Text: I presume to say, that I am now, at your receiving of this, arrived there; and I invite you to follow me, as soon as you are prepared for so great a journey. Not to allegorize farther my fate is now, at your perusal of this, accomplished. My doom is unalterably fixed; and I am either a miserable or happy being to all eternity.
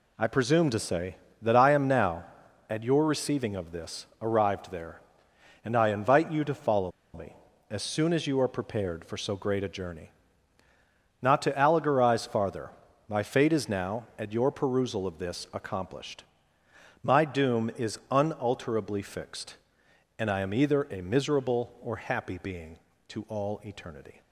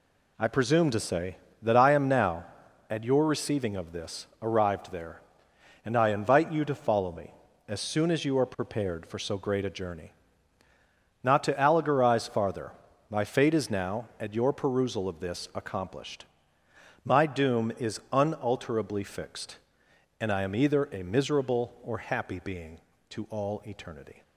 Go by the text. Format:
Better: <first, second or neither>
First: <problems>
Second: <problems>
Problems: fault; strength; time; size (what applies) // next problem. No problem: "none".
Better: second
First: pauses between "follow" and "me"; slight; at 6.9 s; 0.23 s long // pauses between "farther" and "my"; at 12.6 s; 0.40 s long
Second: pauses between "farther" and "my"; at 12.7 s; 0.40 s long